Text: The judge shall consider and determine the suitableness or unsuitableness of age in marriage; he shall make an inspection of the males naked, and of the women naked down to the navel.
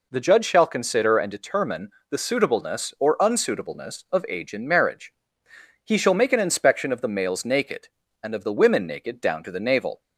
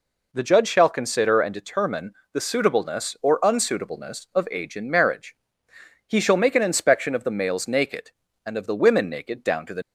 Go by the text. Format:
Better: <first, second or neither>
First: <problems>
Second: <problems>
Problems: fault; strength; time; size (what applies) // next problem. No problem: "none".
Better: first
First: pauses between "determine" and "the"; slight; at 1.9 s; 0.20 s long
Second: pauses between "determine" and "the"; slight; at 2.1 s; 0.20 s long // stops before "navel"; at 9.8 s